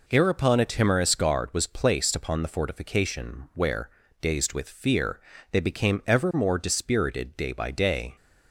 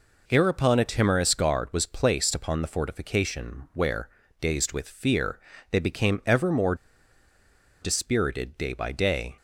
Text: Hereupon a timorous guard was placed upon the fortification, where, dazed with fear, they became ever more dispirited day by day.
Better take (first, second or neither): first